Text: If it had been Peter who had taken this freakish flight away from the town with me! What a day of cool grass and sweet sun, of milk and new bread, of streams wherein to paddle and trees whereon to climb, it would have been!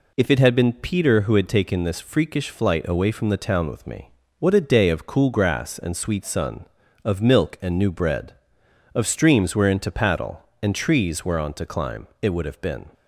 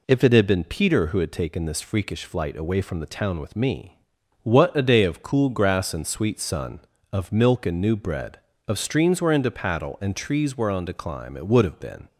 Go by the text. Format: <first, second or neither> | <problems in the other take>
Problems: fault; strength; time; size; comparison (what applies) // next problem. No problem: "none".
neither | none